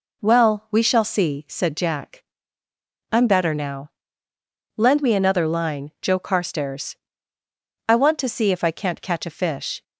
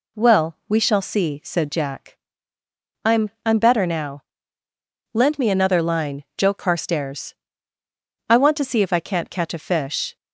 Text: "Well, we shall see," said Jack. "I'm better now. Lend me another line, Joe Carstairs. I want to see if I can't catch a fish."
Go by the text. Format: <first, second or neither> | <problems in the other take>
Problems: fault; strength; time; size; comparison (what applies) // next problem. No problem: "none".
first | says "I'm" twice; at 3.4 s